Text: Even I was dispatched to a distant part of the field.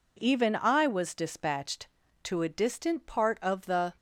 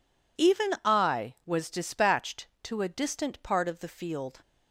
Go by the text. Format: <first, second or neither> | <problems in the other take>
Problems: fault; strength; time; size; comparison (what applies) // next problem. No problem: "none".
second | stops before "field"; at 3.9 s